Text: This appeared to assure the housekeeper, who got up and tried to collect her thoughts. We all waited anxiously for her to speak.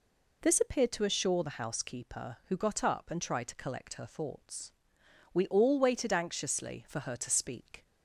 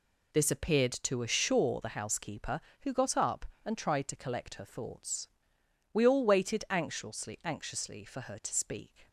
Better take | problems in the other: first | says "anxiously" twice; at 7.4 s

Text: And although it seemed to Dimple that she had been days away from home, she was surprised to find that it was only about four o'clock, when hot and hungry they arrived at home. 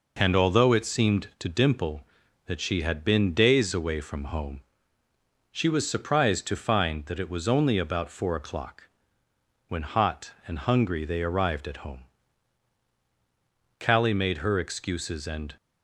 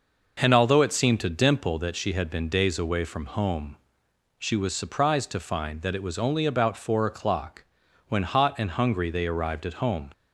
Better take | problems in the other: second | goes on to say "Callie made her excuses and"; strong; from 13.7 s on; 1.7 s long

